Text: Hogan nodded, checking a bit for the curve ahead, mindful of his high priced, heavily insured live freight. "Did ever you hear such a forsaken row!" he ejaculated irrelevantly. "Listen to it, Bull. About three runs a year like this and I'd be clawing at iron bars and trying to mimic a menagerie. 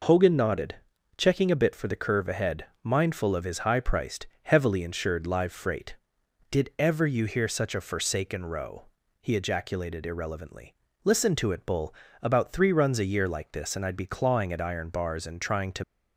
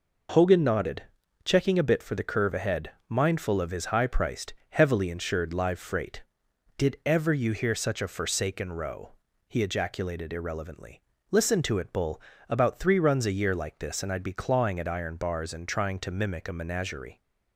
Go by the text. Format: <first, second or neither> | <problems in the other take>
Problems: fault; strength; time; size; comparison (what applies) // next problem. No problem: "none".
second | stops before "mimic a menagerie"; at 15.8 s